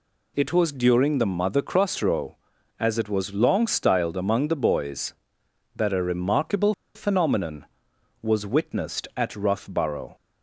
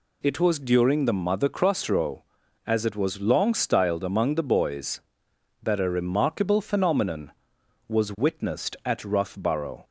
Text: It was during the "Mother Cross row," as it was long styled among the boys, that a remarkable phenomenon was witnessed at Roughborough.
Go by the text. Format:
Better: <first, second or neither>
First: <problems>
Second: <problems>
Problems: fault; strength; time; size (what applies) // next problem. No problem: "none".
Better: second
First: pauses between "remarkable" and "phenomenon"; slight; at 6.7 s; 0.21 s long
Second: none